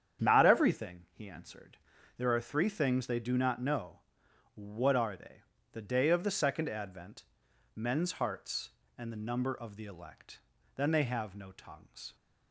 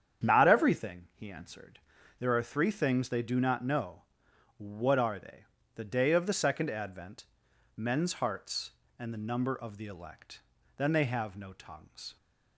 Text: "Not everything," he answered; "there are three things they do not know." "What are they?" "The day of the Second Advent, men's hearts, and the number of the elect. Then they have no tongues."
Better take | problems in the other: neither | starts louder than the rest; strong; the same in both

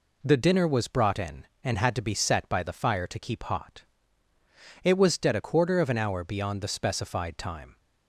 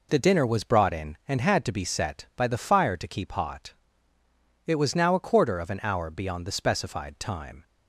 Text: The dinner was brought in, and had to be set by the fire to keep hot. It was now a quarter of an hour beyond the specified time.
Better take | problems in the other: second | says "dead" for "now"; at 5.1 s

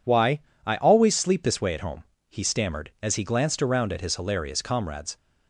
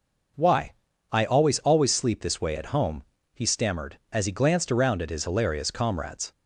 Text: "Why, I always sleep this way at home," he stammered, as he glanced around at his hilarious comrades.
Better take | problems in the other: first | says "always" twice; at 1.5 s

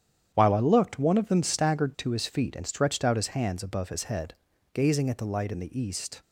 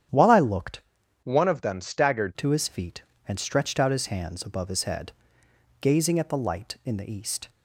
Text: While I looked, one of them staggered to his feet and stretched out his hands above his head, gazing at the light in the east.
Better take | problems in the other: first | starts louder than the rest; strong; until 1.5 s; 9.5 dB; strong in the first // changes voice from "one" to "staggered"; from 1.2 to 2.3 s; 1.1 s long

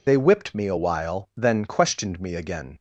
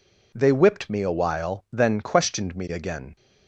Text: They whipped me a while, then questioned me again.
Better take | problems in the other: second | loses the start of "They"; at 0.0 s; 80 ms

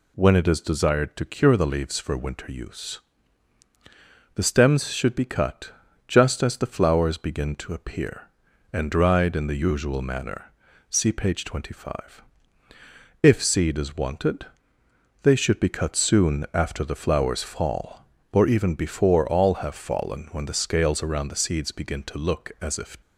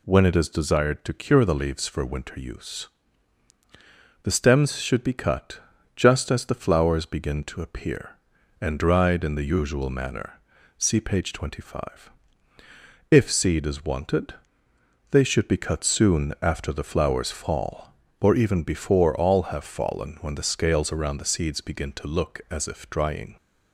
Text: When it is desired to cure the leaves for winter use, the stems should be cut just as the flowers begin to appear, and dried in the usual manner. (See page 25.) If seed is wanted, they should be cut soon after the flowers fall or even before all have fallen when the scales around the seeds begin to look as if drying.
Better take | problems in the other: second | pauses between "cut" and "just"; slight; at 5.7 s; 0.34 s long; slight in the second // stops before "drying"; at 23.0 s

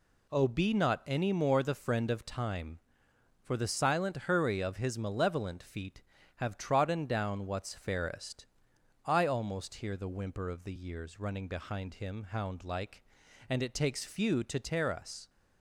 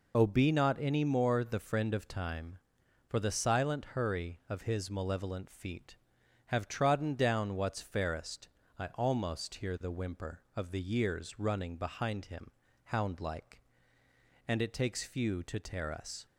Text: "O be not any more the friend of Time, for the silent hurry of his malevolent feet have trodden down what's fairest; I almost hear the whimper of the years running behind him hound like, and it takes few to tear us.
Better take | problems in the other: first | loses the start of "O"; at 0.1 s; 20 ms // pauses between "him" and "hound"; slight; at 12.4 s; 0.36 s long

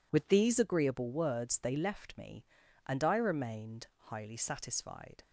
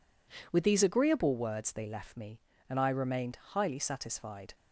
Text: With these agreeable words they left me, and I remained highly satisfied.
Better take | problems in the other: neither | none

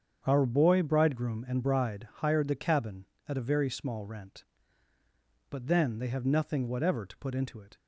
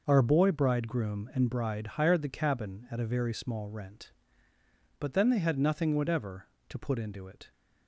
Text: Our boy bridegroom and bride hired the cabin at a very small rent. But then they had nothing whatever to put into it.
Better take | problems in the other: second | starts louder than the rest; strong; until 1.2 s; 7.5 dB // says "have" for "had"; at 6.0 s

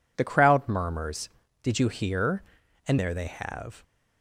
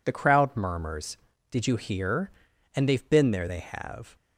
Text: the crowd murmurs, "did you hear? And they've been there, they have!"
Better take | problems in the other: second | skips "they've been"; at 2.9 s

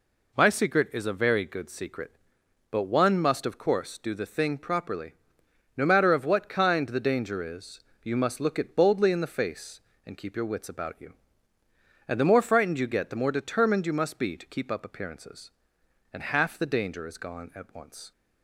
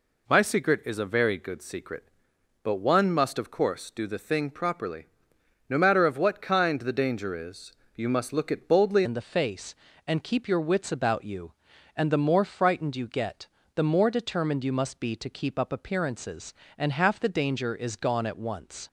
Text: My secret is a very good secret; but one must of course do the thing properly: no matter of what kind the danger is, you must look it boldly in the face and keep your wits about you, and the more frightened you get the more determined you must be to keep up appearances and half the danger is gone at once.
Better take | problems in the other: first | changes voice at "in"; from 9.0 s on; 9.8 s long // pauses between "get" and "the"; slight; at 13.4 s; 0.28 s long

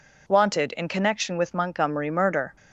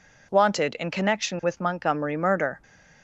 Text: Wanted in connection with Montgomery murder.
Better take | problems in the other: neither | none

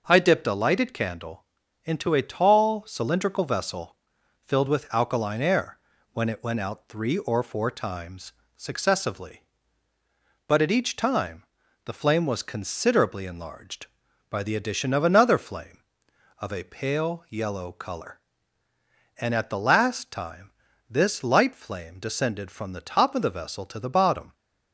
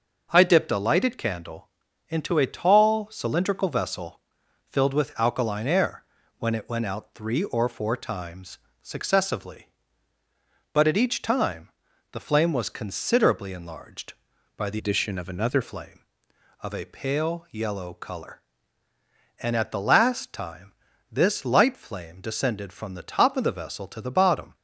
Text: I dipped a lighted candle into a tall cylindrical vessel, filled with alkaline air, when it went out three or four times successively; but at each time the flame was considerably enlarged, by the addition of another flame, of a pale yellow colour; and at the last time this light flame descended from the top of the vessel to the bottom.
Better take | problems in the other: first | starts louder than the rest; noticeable; until 1.3 s; 6 dB // pauses between "candle" and "into"; at 1.6 s; 0.42 s long; also in the first // pauses between "times" and "successively"; slight; at 8.5 s; 0.24 s long; slight in the first // pauses between "time" and "the"; at 11.7 s; 0.42 s long; also in the first // changes voice from "addition" to "another"; from 14.7 to 15.6 s; 0.9 s long // pauses between "time" and "this"; at 20.7 s; 0.40 s long; also in the first

